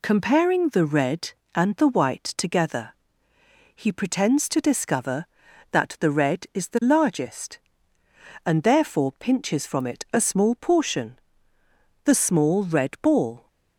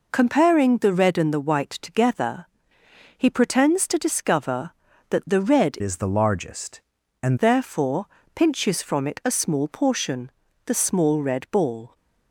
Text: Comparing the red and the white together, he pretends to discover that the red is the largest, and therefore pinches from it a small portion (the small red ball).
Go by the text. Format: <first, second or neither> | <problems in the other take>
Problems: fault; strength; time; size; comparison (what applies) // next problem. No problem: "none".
first | changes voice from "is" to "and"; from 5.8 to 7.3 s; 1.5 s long // pauses between "therefore" and "pinches"; slight; at 8.0 s; 0.26 s long